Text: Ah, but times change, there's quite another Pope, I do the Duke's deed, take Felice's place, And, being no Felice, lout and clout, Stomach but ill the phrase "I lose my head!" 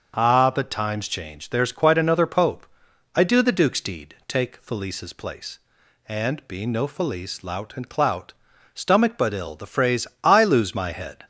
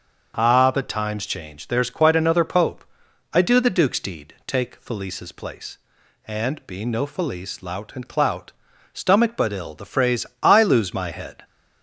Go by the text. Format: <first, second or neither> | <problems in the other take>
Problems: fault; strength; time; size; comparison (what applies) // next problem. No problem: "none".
neither | starts louder than the rest; the same in both // pauses between "phrase" and "I"; slight; the same in both